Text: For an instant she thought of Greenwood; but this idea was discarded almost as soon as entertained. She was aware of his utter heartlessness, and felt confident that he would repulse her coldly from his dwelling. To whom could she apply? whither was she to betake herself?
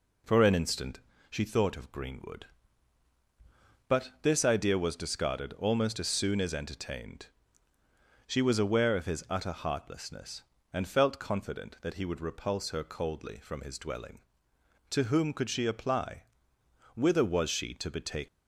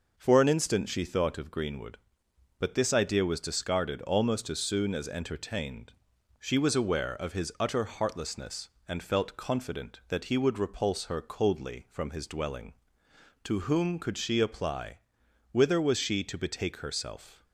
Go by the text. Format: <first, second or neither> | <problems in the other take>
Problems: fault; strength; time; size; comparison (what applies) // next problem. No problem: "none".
second | pauses between "instant" and "she"; slight; at 1.0 s; 0.28 s long // stops before "herself"; at 18.2 s